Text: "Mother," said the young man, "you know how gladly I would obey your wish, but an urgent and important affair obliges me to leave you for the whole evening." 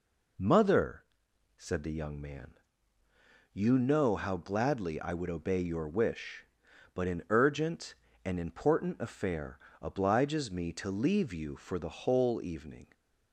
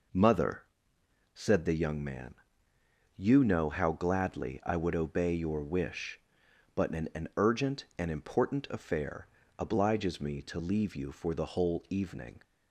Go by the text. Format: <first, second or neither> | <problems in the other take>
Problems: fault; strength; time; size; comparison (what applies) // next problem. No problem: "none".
first | says "an" twice; at 7.1 s // pauses between "affair" and "obliges"; slight; at 9.2 s; 0.32 s long; slight in the first